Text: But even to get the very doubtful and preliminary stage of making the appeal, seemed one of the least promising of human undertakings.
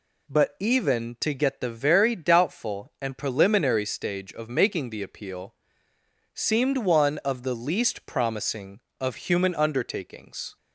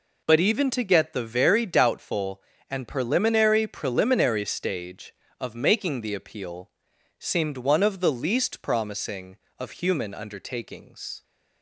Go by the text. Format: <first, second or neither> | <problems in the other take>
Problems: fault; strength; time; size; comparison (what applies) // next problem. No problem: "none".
first | says "preliminary" twice; at 3.6 s